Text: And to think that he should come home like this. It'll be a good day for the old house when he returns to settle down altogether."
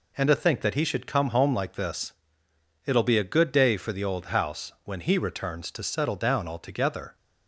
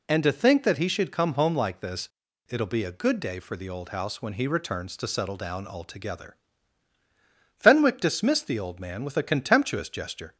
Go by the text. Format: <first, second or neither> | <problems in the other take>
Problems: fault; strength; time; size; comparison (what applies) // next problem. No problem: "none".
first | goes on to say "Fenwick dismissed the old man with a contemptuous gesture"; strong; from 7.5 s on; 2.8 s long